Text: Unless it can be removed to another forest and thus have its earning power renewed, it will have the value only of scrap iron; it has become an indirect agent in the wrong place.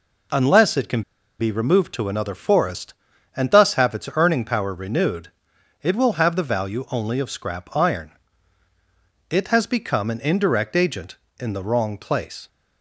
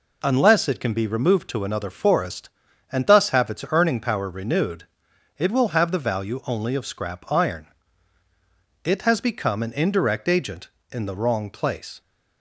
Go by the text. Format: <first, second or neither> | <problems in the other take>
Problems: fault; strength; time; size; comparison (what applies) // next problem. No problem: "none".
second | pauses between "can" and "be"; at 1.0 s; 0.37 s long